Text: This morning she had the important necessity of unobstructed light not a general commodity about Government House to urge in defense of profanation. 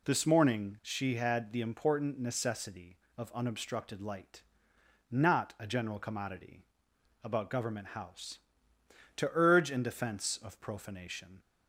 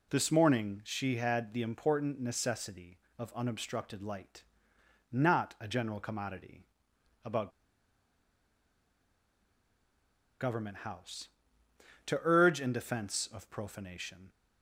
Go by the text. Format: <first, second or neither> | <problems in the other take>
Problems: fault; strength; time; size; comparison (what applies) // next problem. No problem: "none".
first | pauses between "light" and "not"; noticeable; at 4.4 s; 0.68 s long; noticeable in the first // pauses between "commodity" and "about"; noticeable; at 6.6 s; 0.60 s long; noticeable in the first // pauses between "about" and "Government"; strong; at 7.5 s; 2.8 s long